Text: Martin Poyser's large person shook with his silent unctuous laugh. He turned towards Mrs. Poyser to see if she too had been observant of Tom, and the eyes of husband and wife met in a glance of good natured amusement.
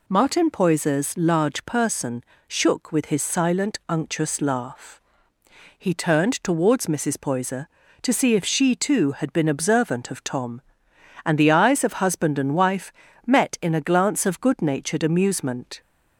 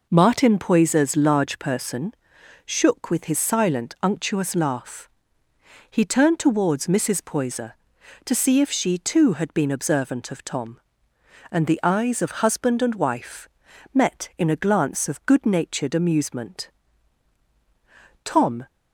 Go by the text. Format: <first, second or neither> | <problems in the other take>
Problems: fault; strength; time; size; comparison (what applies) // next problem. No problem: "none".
first | pauses between "person" and "shook"; noticeable; at 2.1 s; 0.50 s long; slight in the first // pauses between "wife" and "met"; at 13.4 s; 0.44 s long; slight in the first // goes on to say "Tom"; slight; from 18.2 s on; 0.44 s long